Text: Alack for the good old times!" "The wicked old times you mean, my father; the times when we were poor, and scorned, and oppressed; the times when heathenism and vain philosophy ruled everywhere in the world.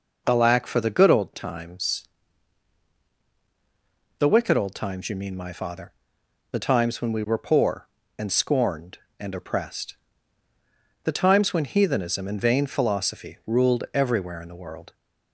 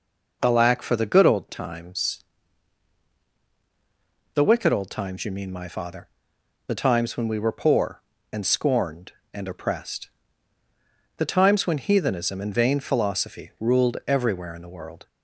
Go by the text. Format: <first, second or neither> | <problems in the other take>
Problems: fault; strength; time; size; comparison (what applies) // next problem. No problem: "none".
neither | none